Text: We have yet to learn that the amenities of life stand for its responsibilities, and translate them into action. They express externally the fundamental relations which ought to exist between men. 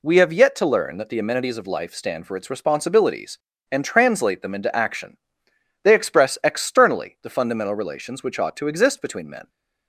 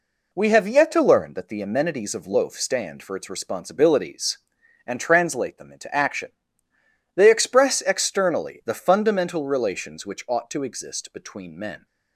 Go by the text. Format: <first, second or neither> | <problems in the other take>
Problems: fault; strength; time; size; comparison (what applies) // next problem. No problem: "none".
first | says "loaf" for "life"; at 2.2 s